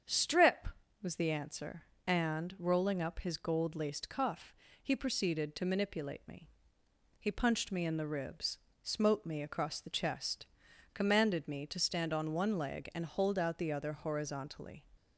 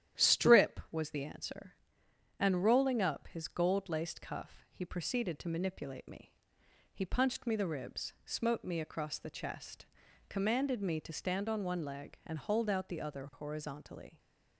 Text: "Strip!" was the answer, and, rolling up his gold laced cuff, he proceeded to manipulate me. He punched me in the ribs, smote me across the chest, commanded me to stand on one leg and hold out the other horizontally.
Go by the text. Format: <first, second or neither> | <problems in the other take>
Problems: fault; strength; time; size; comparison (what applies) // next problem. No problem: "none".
first | starts louder than the rest; strong; until 1.2 s; 11 dB; strong in the first // skips "in"; at 7.5 s